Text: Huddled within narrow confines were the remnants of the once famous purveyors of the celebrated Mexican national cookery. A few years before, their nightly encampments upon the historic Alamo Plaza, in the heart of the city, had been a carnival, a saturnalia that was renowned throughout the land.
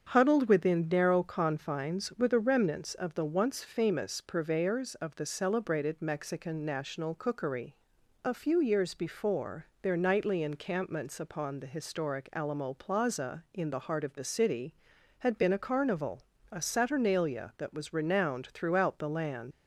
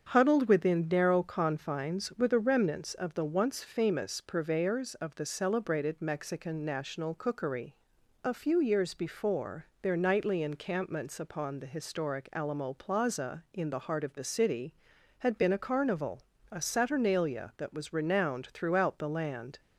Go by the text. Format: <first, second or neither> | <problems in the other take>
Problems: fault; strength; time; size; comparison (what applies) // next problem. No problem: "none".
second | starts louder than the rest; strong; until 1.1 s; 7.5 dB; strong in the second // leaves "land" unfinished; at 19.5 s; 85 ms